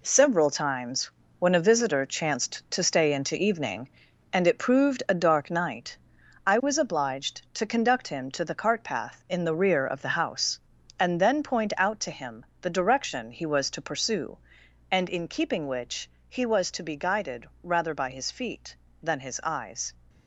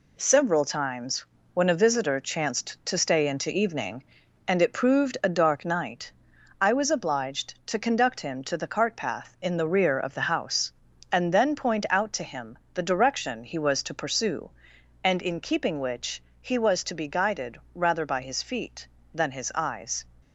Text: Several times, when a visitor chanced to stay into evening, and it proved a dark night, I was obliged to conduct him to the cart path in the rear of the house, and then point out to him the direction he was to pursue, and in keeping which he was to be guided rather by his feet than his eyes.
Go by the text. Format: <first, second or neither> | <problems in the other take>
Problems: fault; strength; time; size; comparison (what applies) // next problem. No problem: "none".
second | gets quieter; strong; throughout; 8.5 dB // pauses between "him" and "the"; slight; at 12.4 s; 0.16 s long; slight in the second // pauses between "which" and "he"; slight; at 16.0 s; 0.18 s long; slight in the second // pauses between "guided" and "rather"; slight; at 17.4 s; 0.16 s long; slight in the second